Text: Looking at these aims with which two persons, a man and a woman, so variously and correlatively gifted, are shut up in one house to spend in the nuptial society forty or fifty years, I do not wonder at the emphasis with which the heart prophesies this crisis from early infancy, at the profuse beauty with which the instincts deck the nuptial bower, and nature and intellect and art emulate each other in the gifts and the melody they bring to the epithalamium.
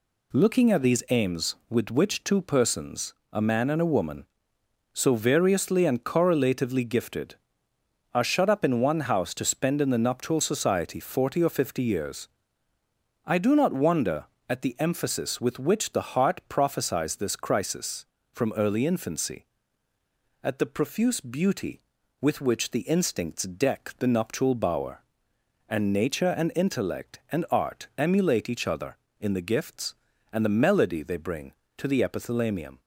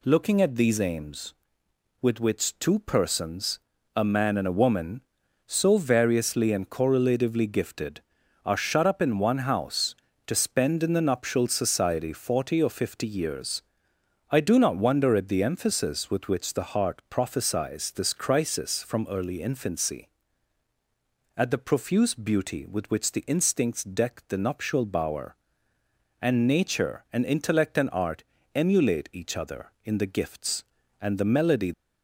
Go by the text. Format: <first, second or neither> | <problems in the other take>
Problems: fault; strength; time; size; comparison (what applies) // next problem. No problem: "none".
first | pauses between "art" and "emulate"; slight; at 28.2 s; 0.32 s long // stops before "they bring to the epithalamium"; at 31.7 s